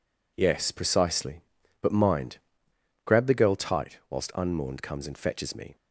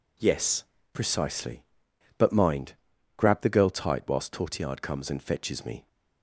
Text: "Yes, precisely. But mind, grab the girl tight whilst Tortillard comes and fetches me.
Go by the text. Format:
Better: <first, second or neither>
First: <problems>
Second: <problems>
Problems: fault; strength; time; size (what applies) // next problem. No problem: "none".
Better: second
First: says "Unmourned" for "Tortillard"; at 4.3 s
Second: none